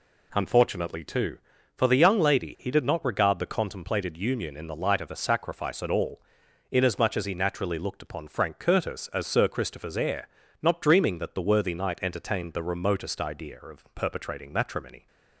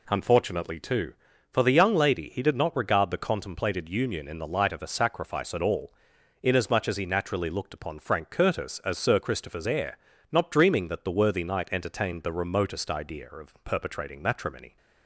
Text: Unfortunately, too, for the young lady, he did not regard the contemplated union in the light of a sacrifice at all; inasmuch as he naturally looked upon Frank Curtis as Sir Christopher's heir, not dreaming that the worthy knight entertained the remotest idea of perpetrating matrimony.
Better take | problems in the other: neither | none

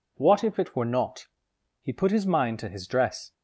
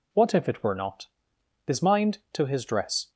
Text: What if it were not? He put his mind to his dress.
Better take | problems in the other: first | skips "He put"; at 1.3 s

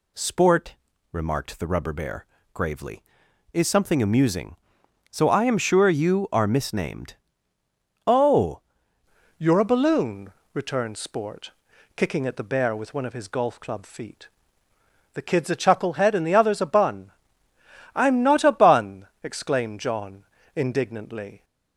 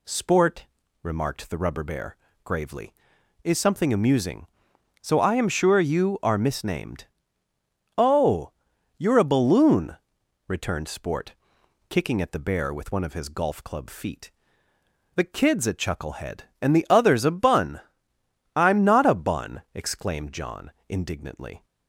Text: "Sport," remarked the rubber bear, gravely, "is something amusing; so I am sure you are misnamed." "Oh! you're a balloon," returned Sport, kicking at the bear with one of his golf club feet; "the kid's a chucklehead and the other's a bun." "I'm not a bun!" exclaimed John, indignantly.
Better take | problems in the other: second | changes voice at "you're"; from 9.3 s on; 12.1 s long

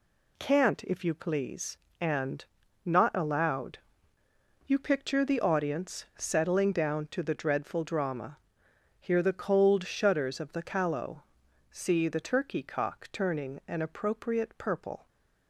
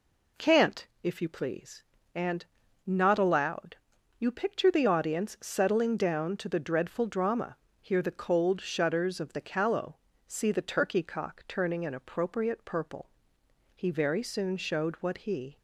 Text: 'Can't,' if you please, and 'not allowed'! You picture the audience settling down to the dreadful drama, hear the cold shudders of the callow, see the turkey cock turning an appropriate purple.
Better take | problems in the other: first | pauses between "and" and "not"; at 2.4 s; 0.44 s long; also in the first // goes on to say "He very soon showed what he"; strong; from 13.7 s on; 1.8 s long

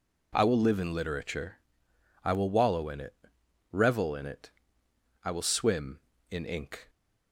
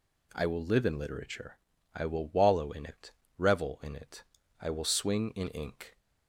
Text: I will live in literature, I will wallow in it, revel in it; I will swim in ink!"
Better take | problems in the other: first | says "swing" for "swim"; at 4.8 s

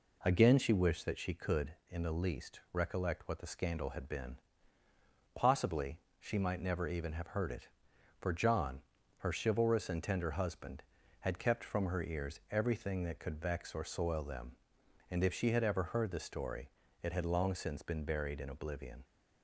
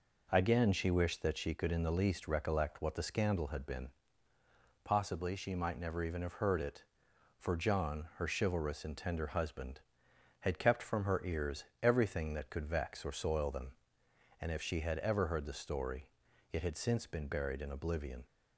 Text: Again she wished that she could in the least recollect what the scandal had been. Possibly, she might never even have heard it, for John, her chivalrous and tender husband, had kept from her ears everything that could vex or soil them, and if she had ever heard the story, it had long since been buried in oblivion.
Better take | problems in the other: first | pauses between "ears" and "everything"; slight; at 11.6 s; 0.18 s long // skips "long"; at 16.7 s

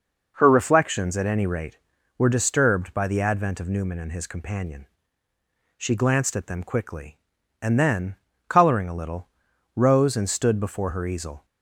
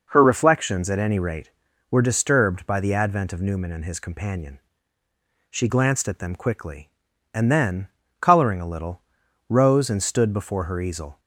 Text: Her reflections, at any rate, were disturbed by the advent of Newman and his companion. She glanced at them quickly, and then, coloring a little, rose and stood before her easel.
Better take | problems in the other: neither | none

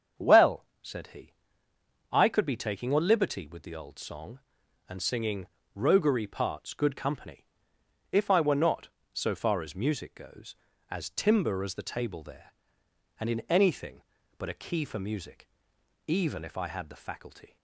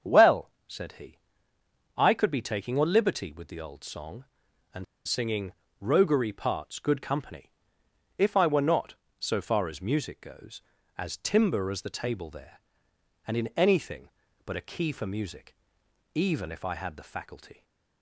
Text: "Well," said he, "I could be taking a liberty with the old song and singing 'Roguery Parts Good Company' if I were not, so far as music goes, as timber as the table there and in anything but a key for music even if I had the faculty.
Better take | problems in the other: first | starts louder than the rest; strong; until 2.0 s; 7.5 dB; strong in the first // pauses between "and" and "singing"; slight; at 4.8 s; 0.22 s long // pauses between "singing" and "Roguery"; slight; at 5.5 s; 0.28 s long; slight in the first // pauses between "Company" and "if"; noticeable; at 7.5 s; 0.66 s long; noticeable in the first // pauses between "music" and "even"; noticeable; at 15.5 s; 0.60 s long; noticeable in the first

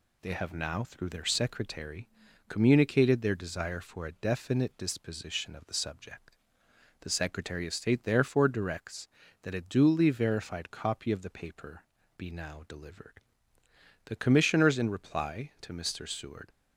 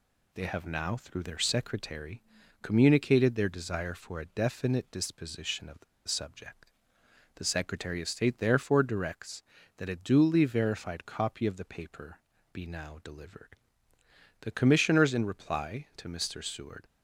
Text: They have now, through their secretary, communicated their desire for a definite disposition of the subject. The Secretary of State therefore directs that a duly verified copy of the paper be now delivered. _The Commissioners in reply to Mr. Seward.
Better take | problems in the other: first | pauses between "the" and "subject"; slight; at 5.8 s; 0.24 s long // pauses between "paper" and "be"; slight; at 12.1 s; 0.34 s long; slight in the first

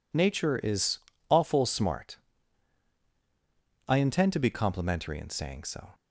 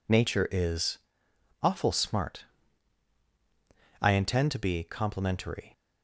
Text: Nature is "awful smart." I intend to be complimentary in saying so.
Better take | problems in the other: first | pauses between "is" and "awful"; noticeable; at 0.9 s; 0.64 s long; slight in the first // stops before "in saying so"; at 5.7 s

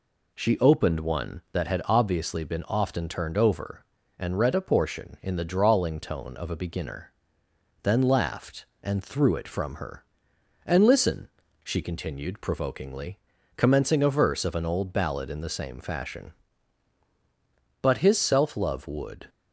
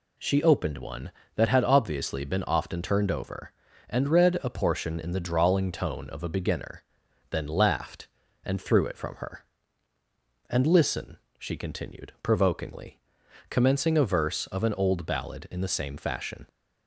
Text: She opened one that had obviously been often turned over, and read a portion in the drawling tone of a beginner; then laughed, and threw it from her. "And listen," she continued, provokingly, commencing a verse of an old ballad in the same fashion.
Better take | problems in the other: second | goes on to say "But his self love would"; from 17.8 s on; 1.4 s long

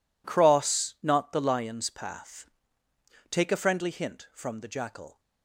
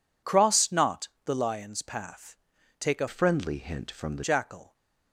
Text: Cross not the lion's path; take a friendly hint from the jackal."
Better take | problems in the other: first | pauses between "not" and "the"; slight; at 1.0 s; 0.16 s long // changes voice from "friendly" to "the"; from 3.0 to 4.2 s; 1.2 s long

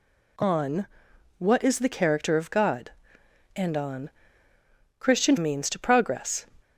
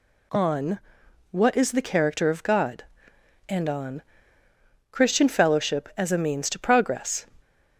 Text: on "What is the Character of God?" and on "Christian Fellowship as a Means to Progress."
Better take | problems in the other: second | pauses between "on" and "What"; noticeable; at 0.8 s; 0.52 s long; noticeable in the second // pauses between "on" and "Christian"; noticeable; at 4.1 s; 0.88 s long; noticeable in the second // skips "Fellowship as a"; at 5.3 s

